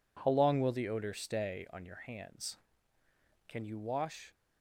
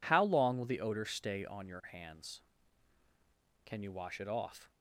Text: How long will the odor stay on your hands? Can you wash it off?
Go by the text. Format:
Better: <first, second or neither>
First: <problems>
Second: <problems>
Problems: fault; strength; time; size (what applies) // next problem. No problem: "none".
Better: second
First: stops before "it off"; at 4.3 s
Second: none